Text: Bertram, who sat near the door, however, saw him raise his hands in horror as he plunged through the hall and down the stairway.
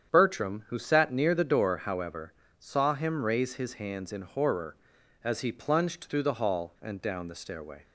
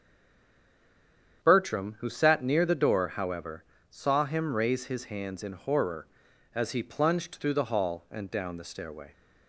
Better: first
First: starts louder than the rest; strong; until 1.1 s; 8.5 dB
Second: stays silent before the first word; noticeable; until 1.4 s; 1.4 s long // starts louder than the rest; strong; until 2.4 s; 8.5 dB

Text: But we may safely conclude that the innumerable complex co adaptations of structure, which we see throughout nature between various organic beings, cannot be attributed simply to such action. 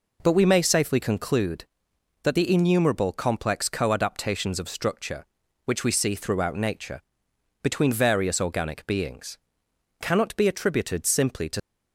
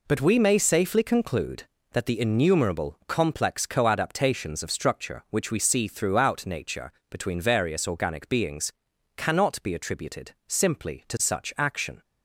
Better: second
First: pauses between "nature" and "between"; noticeable; at 6.9 s; 0.62 s long // stops before "such action"; at 11.5 s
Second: pauses between "nature" and "between"; slight; at 6.9 s; 0.18 s long

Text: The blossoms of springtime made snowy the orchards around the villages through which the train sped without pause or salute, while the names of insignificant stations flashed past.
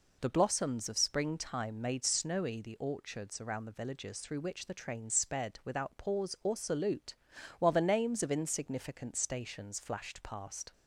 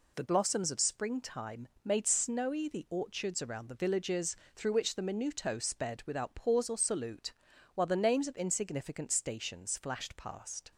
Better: first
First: none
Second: pauses between "springtime" and "made"; slight; at 1.6 s; 0.16 s long // pauses between "villages" and "through"; slight; at 4.3 s; 0.18 s long // says "minuto" for "train"; at 5.0 s

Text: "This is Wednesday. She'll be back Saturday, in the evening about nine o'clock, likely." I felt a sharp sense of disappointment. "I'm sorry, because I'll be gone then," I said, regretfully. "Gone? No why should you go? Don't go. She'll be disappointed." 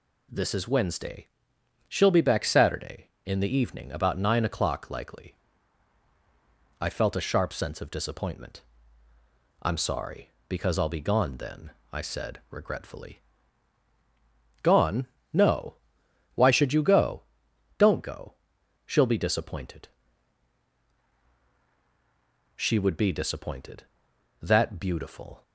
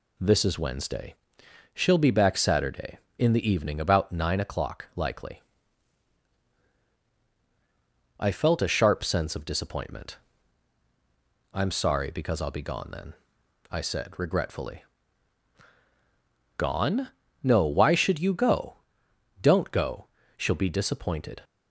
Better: second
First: pauses between "No" and "why"; noticeable; at 15.7 s; 0.58 s long // goes on to say "She would be disappointed that beautiful"; strong; from 22.5 s on; 2.8 s long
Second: none

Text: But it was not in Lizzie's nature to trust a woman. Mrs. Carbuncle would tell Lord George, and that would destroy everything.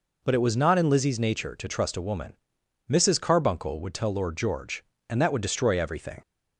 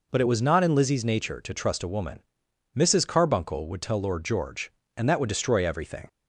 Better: neither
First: none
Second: none

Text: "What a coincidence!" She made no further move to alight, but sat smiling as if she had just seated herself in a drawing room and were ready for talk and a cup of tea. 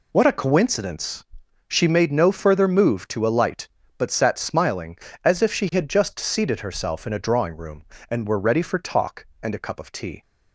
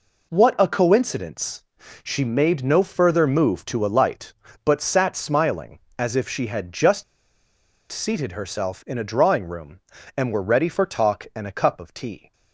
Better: first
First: none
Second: pauses between "just" and "seated"; noticeable; at 7.0 s; 0.88 s long

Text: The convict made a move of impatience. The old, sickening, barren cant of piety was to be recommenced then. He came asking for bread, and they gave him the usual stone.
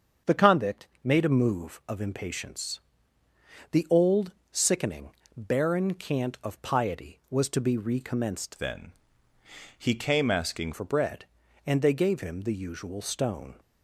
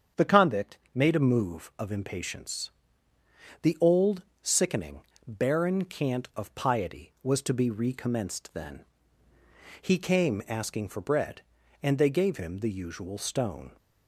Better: second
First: starts louder than the rest; until 1.4 s; 7 dB // pauses between "convict" and "made"; slight; at 0.8 s; 0.16 s long // changes voice from "then" to "asking"; from 8.5 to 10.7 s; 2.2 s long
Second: starts louder than the rest; strong; until 1.3 s; 7.5 dB // pauses between "convict" and "made"; slight; at 0.7 s; 0.16 s long

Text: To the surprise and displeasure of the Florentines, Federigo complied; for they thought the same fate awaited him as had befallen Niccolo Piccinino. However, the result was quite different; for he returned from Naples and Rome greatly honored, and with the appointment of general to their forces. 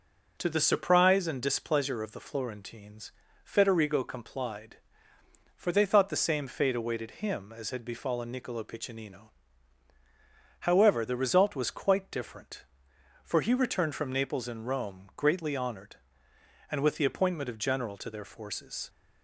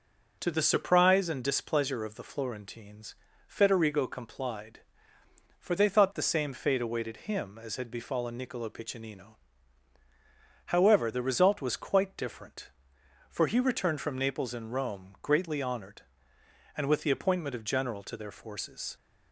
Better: neither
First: none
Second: none

